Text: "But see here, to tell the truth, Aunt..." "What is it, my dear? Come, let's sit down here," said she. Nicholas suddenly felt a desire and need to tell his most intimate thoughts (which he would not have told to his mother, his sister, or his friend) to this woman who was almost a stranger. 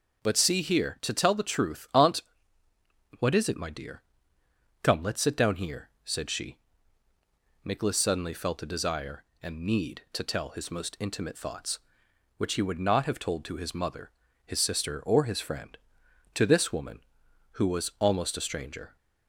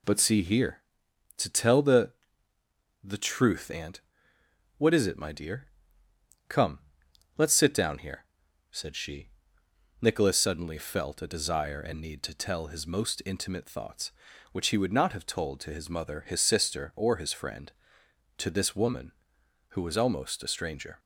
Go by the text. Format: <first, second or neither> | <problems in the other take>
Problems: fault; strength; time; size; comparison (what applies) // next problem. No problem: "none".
first | says "the" twice; at 3.0 s